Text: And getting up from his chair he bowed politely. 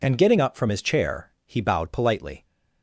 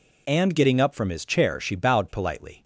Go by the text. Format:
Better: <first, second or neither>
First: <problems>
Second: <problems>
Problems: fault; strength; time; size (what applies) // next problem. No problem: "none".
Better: first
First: none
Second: says "she" for "he"; at 1.5 s